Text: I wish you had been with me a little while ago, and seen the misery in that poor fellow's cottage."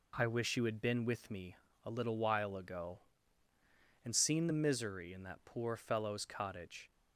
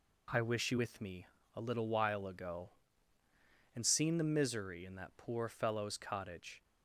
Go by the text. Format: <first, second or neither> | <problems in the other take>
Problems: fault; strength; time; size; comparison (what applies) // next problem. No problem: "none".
first | skips "had been"; at 0.7 s // pauses between "me" and "a"; slight; at 1.2 s; 0.28 s long; slight in the first